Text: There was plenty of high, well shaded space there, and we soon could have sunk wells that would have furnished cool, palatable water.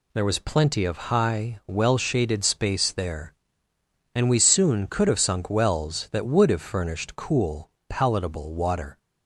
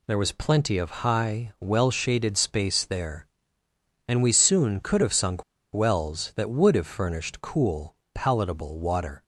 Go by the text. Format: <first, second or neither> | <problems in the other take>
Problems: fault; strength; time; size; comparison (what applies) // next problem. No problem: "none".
first | pauses between "sunk" and "wells"; slight; at 5.4 s; 0.31 s long